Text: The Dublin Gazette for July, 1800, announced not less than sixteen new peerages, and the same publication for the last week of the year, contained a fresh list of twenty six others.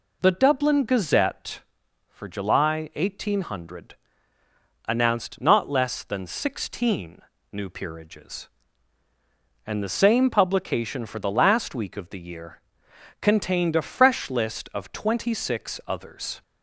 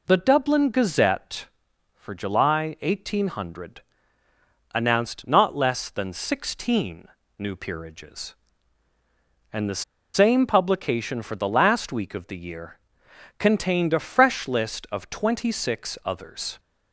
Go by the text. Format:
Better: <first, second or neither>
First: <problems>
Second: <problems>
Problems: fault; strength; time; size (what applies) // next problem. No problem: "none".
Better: first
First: pauses between "sixteen" and "new"; slight; at 7.2 s; 0.32 s long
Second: pauses between "sixteen" and "new"; slight; at 7.0 s; 0.32 s long // pauses between "the" and "same"; slight; at 9.8 s; 0.32 s long